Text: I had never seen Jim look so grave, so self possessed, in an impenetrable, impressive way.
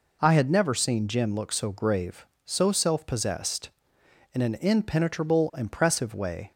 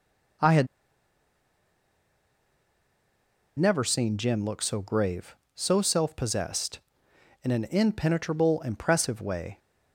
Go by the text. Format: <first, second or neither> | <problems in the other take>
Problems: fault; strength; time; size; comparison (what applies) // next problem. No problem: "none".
first | pauses between "had" and "never"; strong; at 0.6 s; 2.9 s long